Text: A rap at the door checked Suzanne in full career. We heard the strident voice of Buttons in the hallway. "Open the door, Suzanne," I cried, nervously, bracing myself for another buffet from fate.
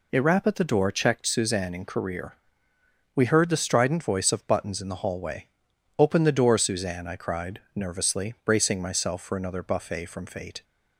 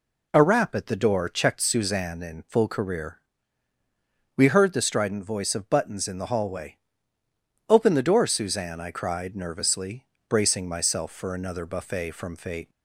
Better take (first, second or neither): second